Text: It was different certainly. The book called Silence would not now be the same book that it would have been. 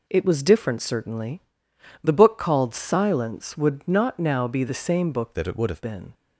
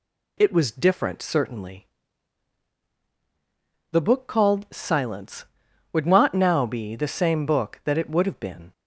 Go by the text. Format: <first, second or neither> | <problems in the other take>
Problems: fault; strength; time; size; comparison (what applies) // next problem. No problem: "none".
second | changes voice from "that" to "have"; from 5.3 to 5.8 s; 0.5 s long